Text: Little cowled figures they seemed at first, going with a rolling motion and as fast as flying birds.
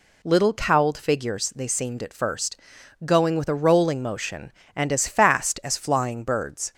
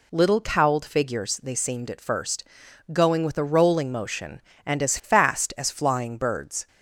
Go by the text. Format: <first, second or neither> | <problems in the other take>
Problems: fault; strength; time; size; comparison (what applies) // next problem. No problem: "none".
neither | none